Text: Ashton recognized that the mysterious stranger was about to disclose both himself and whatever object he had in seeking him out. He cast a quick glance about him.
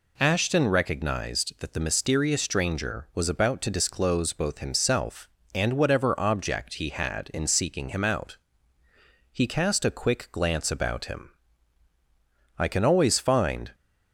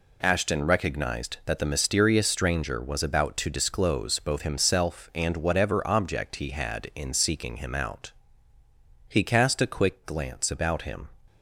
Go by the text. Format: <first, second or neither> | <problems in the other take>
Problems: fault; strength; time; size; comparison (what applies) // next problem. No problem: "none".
second | goes on to say "I can always find"; noticeable; from 12.5 s on; 1.1 s long